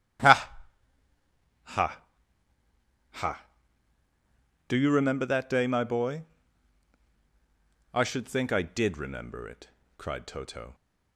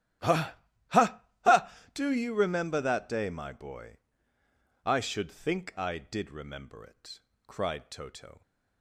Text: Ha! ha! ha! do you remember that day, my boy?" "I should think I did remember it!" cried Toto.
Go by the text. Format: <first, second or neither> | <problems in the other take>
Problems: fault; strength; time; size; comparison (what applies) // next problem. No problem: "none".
neither | starts louder than the rest; strong; the same in both